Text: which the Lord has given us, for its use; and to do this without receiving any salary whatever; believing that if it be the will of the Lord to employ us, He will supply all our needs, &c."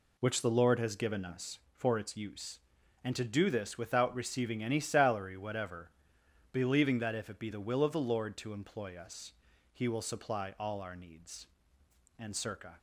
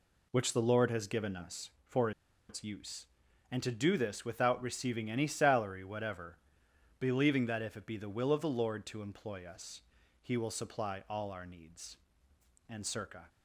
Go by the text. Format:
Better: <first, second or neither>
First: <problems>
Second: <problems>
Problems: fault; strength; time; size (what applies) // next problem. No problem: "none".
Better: first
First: none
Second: pauses between "for" and "its"; at 2.1 s; 0.38 s long